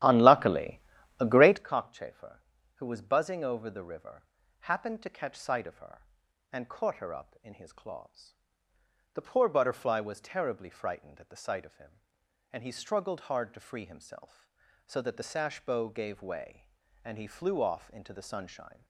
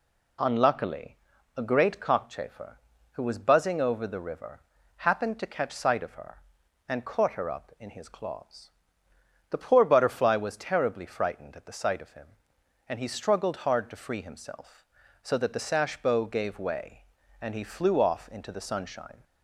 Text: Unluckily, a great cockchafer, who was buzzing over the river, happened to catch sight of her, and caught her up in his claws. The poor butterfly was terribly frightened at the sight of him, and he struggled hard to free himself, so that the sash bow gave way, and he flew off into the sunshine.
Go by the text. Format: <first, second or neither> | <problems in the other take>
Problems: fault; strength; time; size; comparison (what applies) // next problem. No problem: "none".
second | starts louder than the rest; strong; until 1.6 s; 12.5 dB